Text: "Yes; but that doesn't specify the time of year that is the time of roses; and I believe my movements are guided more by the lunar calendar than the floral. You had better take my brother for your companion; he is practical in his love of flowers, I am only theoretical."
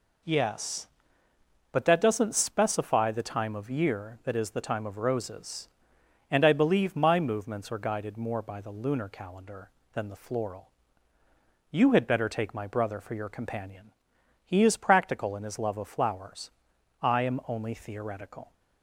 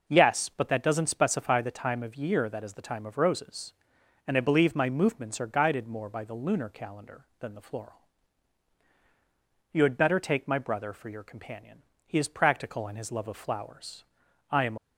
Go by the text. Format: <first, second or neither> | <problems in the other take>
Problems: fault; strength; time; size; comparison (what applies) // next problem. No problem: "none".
first | stops before "only theoretical"; at 14.7 s